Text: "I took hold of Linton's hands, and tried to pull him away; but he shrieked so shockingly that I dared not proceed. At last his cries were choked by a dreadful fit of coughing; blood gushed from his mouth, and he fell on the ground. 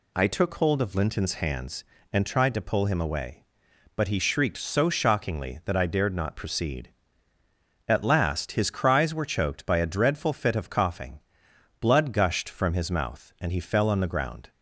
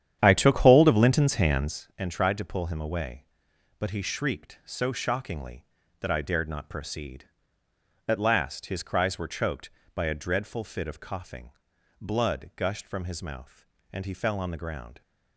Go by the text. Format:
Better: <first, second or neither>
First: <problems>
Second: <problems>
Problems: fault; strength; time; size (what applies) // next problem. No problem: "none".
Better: first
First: none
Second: starts louder than the rest; strong; until 1.8 s; 10 dB